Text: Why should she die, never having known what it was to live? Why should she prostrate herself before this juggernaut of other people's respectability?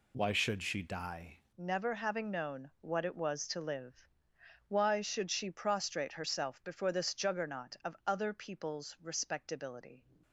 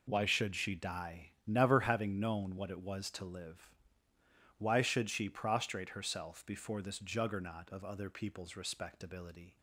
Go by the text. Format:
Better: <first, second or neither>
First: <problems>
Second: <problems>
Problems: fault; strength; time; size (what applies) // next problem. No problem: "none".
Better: second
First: changes voice at "never"; from 1.5 s on; 8.5 s long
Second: none